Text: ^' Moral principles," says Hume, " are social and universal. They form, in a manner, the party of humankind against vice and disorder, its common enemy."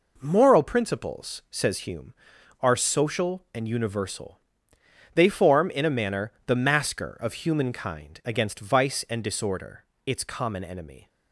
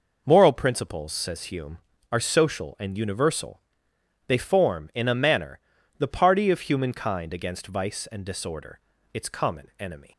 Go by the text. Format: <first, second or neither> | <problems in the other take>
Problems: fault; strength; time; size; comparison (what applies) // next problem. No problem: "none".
second | says "masker" for "party"; at 6.5 s